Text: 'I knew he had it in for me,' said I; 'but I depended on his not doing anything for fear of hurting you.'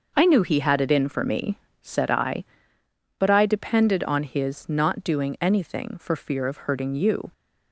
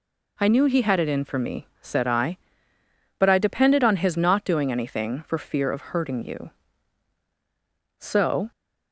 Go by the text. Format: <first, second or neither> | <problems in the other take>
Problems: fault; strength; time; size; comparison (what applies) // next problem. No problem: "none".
first | goes on to say "So"; from 8.0 s on; 0.50 s long